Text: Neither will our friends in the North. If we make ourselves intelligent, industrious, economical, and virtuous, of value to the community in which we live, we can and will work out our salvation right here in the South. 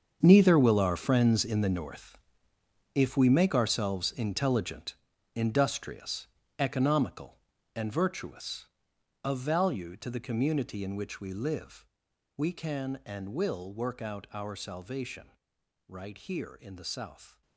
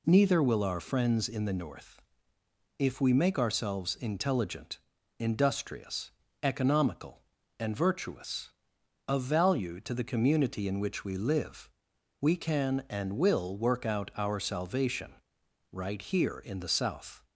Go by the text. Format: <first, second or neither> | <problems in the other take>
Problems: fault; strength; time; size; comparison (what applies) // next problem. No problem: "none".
second | gets quieter; strong; throughout; 14 dB // pauses between "salvation" and "right"; noticeable; at 15.2 s; 0.58 s long; noticeable in the second